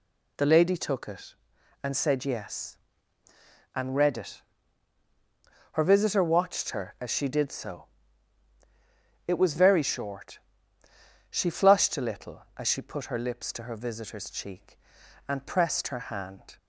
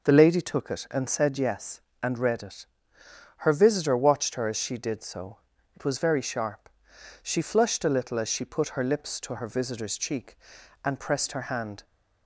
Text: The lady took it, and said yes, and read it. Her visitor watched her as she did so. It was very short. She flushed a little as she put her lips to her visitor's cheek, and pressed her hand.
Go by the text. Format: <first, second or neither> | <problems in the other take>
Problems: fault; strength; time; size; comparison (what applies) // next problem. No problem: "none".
first | says "sharp" for "short"; at 6.2 s